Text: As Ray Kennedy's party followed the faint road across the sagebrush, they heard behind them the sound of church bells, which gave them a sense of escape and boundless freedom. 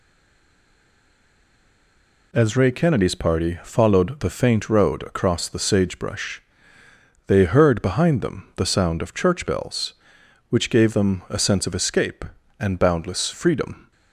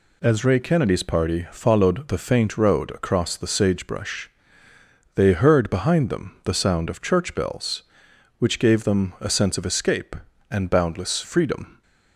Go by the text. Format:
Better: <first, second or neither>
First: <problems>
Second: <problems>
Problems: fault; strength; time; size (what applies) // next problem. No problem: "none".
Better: second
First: stays silent before the first word; until 2.3 s; 2.3 s long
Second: none